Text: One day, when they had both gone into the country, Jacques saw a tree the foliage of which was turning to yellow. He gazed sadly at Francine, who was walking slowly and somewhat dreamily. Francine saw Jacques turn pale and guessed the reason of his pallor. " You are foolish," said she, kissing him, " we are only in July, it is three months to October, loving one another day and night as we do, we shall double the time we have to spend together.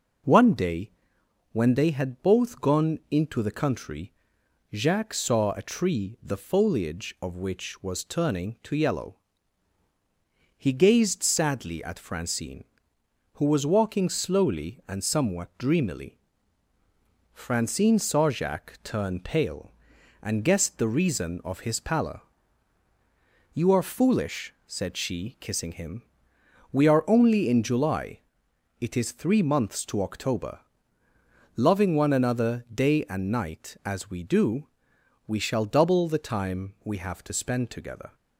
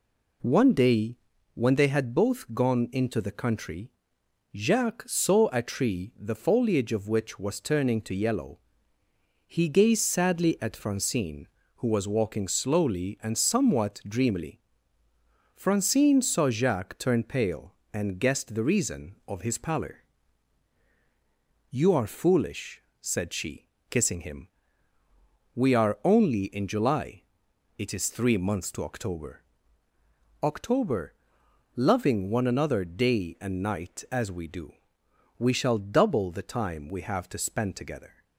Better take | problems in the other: first | says "October" twice; at 30.4 s

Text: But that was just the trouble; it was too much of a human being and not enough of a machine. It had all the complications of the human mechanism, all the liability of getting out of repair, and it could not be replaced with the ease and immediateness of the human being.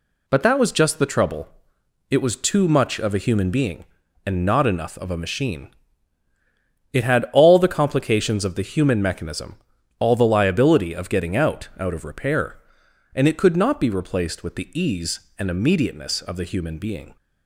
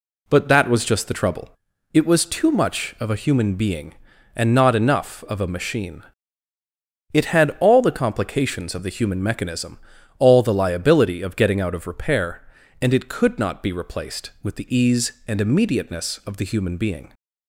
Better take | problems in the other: second | says "out" twice; at 11.7 s

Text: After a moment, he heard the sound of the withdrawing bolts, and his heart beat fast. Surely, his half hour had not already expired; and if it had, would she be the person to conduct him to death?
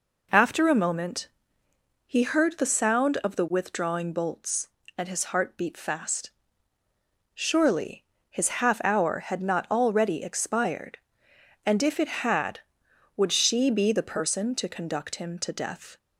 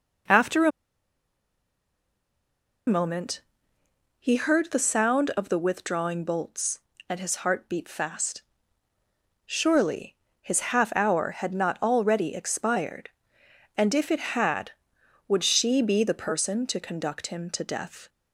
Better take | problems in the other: first | pauses between "a" and "moment"; strong; at 0.7 s; 2.1 s long // pauses between "his" and "half"; slight; at 10.5 s; 0.16 s long; slight in the first

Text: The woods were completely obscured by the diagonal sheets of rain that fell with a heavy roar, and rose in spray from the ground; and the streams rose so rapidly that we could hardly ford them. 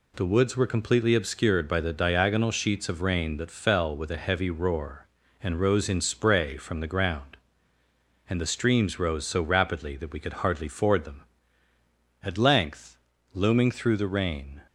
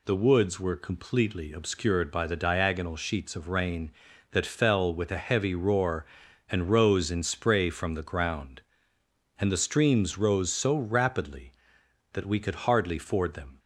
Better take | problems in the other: second | goes on to say "At length looming through the rain"; strong; from 12.2 s on; 2.3 s long

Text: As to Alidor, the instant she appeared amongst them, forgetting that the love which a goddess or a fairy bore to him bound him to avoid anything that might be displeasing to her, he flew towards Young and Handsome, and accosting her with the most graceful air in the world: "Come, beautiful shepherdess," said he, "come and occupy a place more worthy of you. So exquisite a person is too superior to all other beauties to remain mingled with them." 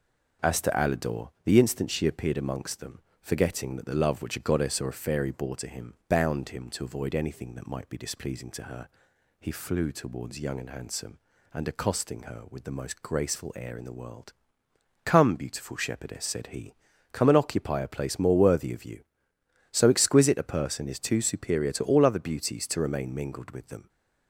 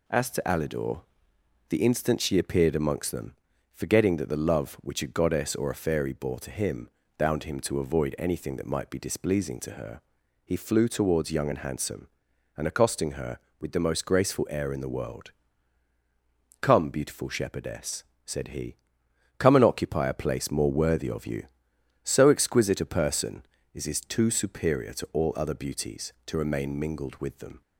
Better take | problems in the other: first | pauses between "him" and "bound"; slight; at 6.8 s; 0.30 s long // says "is" twice; at 23.8 s

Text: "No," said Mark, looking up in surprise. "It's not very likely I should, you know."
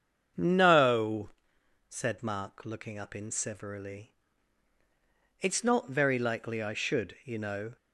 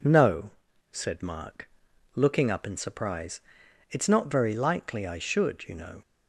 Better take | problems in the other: second | starts louder than the rest; strong; until 1.9 s; 7.5 dB // says "severally" for "surprise"; at 3.2 s

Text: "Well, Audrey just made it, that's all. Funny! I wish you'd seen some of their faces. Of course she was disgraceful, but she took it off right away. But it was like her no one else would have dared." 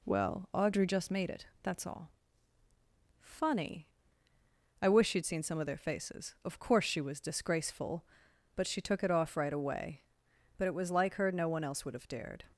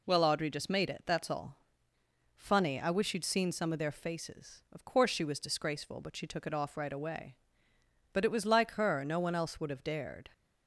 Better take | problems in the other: neither | none

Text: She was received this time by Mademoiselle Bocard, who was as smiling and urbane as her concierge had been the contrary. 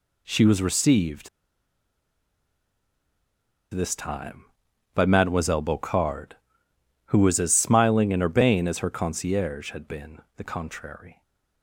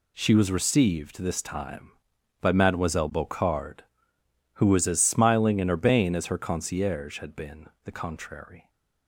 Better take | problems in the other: second | pauses between "received" and "this"; strong; at 1.2 s; 2.4 s long // pauses between "been" and "the"; slight; at 10.1 s; 0.16 s long; slight in the second

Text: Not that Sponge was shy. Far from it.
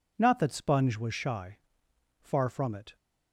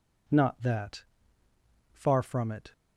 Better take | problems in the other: first | skips "Sponge was shy"; at 1.4 s

